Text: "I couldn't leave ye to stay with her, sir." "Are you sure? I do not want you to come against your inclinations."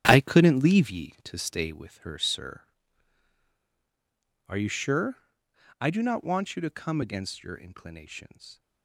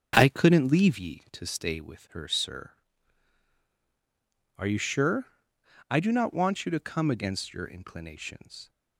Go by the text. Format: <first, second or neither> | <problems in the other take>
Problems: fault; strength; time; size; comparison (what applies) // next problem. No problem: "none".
second | gets quieter; strong; throughout; 12 dB // starts louder than the rest; strong; until 1.0 s; 11.5 dB; strong in the second